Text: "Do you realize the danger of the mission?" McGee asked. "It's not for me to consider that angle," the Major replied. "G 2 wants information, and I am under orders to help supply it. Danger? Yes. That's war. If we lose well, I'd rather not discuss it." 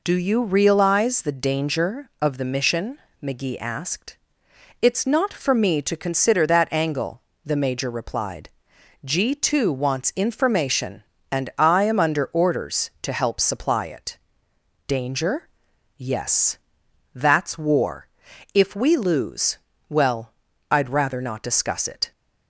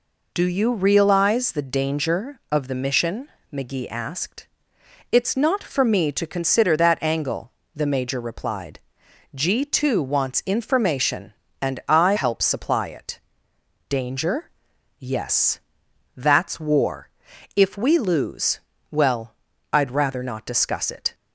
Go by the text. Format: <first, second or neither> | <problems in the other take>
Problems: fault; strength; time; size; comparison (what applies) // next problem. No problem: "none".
first | skips "am under orders to"; at 12.1 s // pauses between "lose" and "well"; slight; at 18.6 s; 0.30 s long; slight in the first